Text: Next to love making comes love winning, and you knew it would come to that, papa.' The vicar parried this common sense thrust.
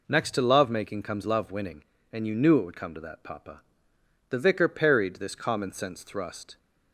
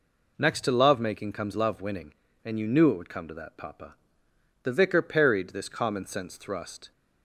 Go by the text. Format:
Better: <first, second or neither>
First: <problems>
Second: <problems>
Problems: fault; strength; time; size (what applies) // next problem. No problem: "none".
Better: neither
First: none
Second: none